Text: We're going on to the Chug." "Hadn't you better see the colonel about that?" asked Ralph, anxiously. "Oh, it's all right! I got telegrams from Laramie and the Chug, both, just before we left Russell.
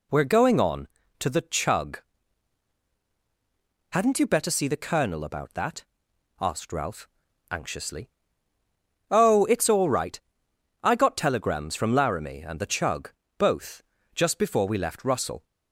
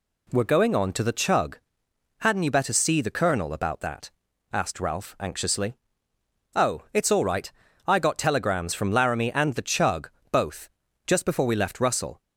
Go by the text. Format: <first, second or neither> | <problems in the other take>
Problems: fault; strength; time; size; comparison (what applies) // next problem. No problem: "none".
neither | none